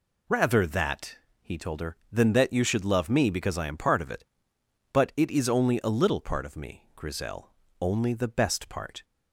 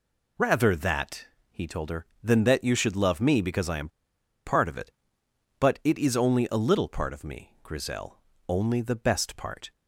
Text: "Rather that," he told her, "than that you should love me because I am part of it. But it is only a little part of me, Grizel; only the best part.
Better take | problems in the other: first | pauses between "am" and "part"; noticeable; at 3.8 s; 0.57 s long

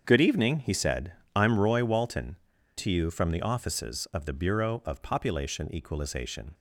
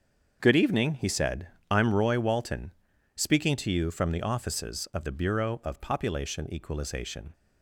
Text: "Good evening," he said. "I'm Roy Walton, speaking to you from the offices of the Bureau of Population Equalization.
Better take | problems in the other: second | starts louder than the rest; until 1.0 s; 7 dB; also in the second // skips "speaking"; at 2.5 s

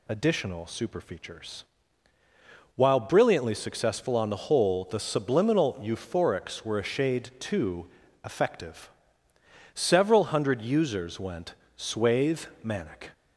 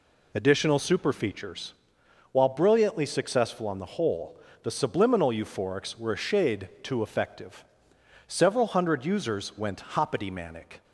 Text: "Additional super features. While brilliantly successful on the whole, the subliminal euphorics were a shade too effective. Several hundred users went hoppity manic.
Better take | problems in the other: second | pauses between "too" and "effective"; slight; at 7.8 s; 0.36 s long // says "swathe" for "hoppity"; at 11.7 s

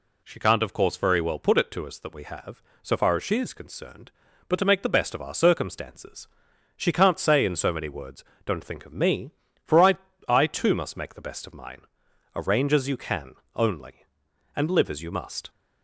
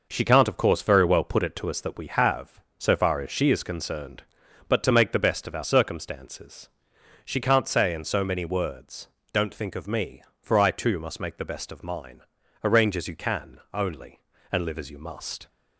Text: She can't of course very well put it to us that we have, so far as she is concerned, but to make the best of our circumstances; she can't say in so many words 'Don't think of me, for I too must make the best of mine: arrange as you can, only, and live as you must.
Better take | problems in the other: second | pauses between "words" and "Don't"; slight; at 8.2 s; 0.22 s long; slight in the second // says "I" twice; at 10.2 s

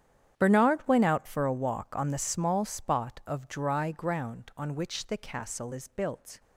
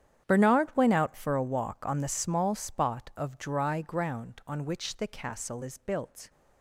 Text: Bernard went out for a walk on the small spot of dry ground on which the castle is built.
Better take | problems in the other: neither | starts louder than the rest; strong; the same in both

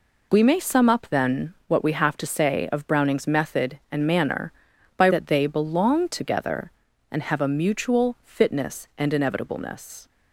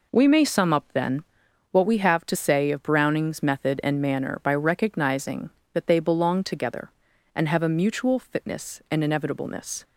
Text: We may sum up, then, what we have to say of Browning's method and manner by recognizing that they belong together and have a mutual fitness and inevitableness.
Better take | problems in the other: second | skips "recognizing"; at 5.0 s

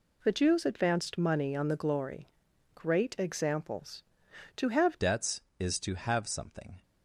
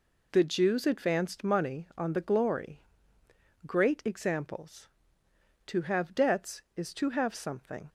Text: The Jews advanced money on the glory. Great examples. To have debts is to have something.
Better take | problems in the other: second | changes voice at "debts"; from 5.0 s on; 1.8 s long

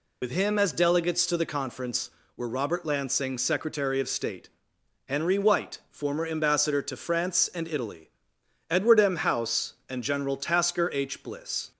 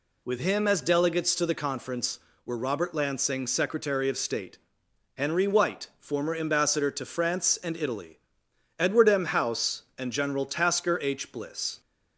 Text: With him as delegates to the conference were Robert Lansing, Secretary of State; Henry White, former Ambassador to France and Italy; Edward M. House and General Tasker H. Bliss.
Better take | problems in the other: second | loses the start of "With"; at 0.2 s; 70 ms

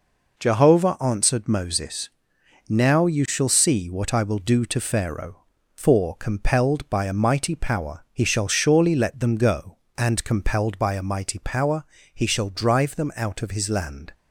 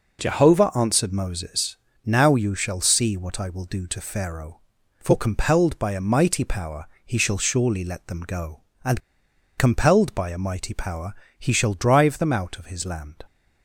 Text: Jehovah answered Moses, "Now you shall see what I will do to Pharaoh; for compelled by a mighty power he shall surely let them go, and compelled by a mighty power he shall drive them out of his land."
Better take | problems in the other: first | pauses between "power" and "he"; slight; at 6.8 s; 0.18 s long // pauses between "and" and "compelled"; noticeable; at 8.9 s; 0.57 s long // pauses between "power" and "he"; slight; at 11.1 s; 0.24 s long; slight in the first

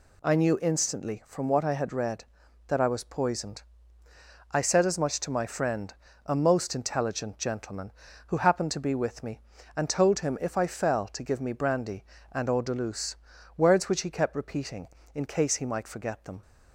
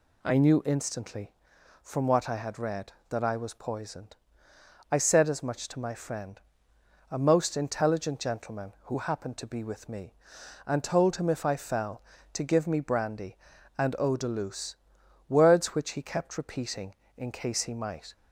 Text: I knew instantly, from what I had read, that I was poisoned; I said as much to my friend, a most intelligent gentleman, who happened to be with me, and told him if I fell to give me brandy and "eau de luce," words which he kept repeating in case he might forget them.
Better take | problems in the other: first | stops before "forget them"; at 18.1 s

